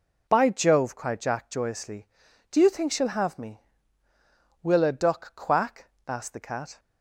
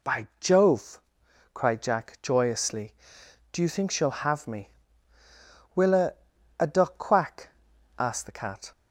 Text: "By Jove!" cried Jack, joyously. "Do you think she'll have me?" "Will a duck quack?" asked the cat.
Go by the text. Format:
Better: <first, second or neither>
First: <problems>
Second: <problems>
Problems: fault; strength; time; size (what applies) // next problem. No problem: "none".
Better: first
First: none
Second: says "a" twice; at 6.5 s